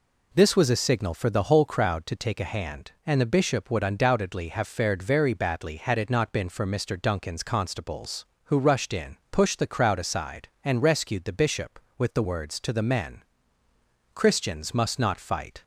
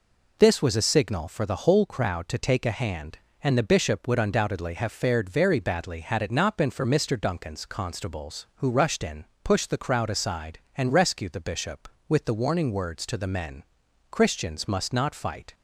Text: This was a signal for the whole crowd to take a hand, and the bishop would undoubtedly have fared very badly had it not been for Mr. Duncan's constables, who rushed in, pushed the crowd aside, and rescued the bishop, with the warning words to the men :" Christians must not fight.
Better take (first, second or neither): second